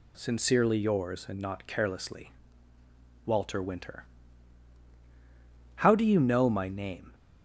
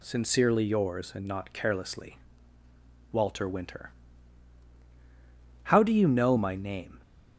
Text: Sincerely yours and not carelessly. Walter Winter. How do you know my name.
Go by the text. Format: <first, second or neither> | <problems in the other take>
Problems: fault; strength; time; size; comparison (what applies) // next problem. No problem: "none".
neither | none